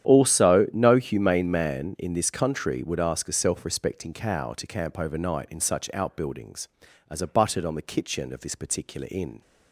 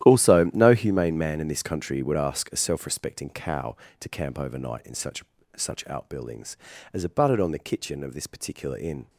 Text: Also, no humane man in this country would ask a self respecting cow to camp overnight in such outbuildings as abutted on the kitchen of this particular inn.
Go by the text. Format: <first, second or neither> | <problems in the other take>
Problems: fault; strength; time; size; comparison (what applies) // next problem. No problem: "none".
first | starts louder than the rest; strong; until 1.0 s; 12 dB; strong in the first // says "such" twice; at 5.5 s